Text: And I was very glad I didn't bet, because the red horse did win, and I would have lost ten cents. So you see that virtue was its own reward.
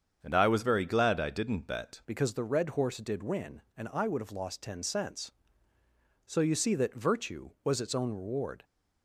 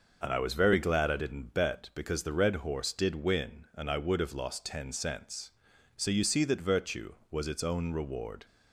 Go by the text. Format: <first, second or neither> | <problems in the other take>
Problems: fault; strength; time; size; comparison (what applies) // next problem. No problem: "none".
second | starts louder than the rest; strong; until 1.2 s; 7.5 dB; noticeable in the second // changes voice at "because"; from 2.0 s on; 6.6 s long